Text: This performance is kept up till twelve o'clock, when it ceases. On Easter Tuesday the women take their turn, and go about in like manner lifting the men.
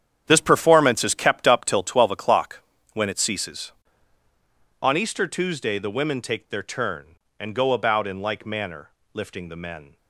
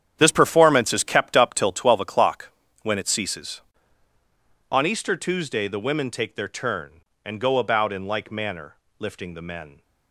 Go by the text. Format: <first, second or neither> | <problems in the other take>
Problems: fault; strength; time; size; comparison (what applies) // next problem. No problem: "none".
neither | starts louder than the rest; strong; the same in both // pauses between "manner" and "lifting"; slight; the same in both